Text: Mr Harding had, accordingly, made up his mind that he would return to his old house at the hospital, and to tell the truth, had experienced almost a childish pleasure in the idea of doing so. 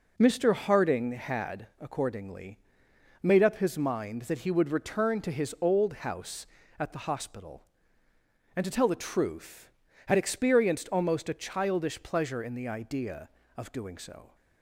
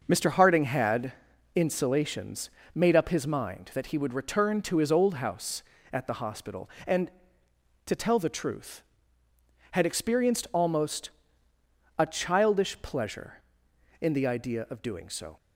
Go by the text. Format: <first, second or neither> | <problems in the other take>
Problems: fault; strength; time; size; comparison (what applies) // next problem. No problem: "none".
first | starts louder than the rest; noticeable; until 1.0 s; 6 dB // says "insulations" for "accordingly"; at 1.5 s // pauses between "almost" and "a"; noticeable; at 11.1 s; 0.88 s long